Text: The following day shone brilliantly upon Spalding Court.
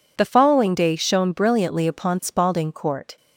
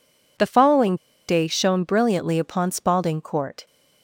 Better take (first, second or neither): first